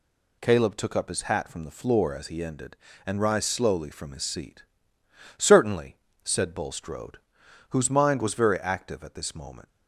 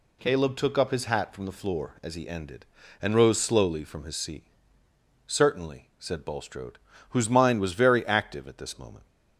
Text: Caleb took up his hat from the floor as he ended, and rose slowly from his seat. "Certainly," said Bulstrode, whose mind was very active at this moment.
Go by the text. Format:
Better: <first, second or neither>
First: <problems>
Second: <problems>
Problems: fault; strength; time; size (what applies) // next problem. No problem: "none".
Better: second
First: says "rise" for "rose"; at 3.2 s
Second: none